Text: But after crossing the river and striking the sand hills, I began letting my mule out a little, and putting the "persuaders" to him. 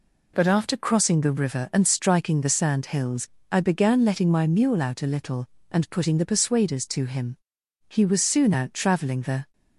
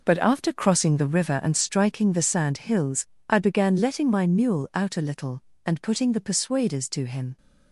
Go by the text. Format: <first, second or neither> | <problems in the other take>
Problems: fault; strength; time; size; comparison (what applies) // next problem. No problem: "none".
second | goes on to say "He was soon out traveling the"; from 7.8 s on; 1.6 s long